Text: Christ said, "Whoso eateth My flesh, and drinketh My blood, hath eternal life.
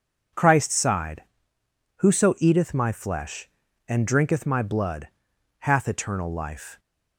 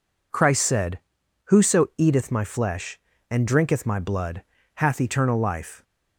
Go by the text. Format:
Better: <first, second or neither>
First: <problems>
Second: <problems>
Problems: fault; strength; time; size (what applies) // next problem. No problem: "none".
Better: second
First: says "sighed" for "said"; at 0.7 s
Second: none